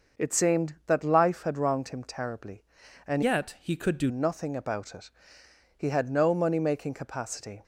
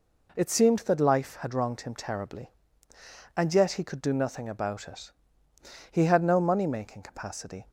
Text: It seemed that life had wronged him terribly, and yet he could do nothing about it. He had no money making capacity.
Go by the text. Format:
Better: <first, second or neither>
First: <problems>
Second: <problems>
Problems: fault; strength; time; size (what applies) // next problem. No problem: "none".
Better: second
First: starts louder than the rest; until 1.2 s; 6 dB // changes voice from "yet" to "do"; from 3.2 to 4.0 s; 0.8 s long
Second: none